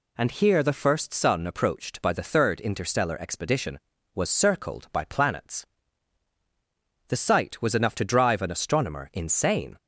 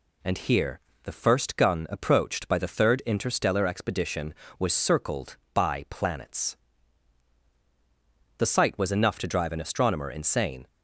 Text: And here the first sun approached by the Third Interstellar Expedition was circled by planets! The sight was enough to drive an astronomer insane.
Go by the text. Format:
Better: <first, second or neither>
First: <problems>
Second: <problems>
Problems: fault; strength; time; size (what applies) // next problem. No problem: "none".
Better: first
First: none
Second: pauses between "here" and "the"; slight; at 0.8 s; 0.22 s long // says "gun" for "sun"; at 1.5 s